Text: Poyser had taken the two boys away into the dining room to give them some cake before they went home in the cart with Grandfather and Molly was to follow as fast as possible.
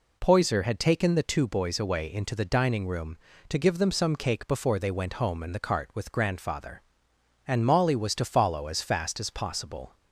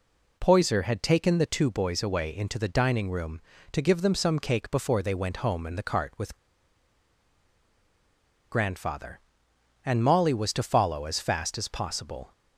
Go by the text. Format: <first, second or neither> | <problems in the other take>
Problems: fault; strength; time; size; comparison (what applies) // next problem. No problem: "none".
first | pauses between "with" and "Grandfather"; strong; at 6.3 s; 2.1 s long